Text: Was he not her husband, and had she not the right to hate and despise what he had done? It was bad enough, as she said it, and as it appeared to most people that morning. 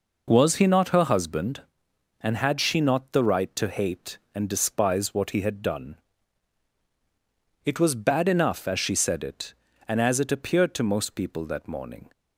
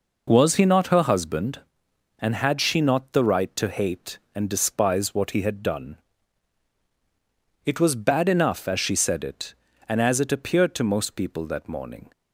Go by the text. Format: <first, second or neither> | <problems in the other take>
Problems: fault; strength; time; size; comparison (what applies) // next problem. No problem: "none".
neither | none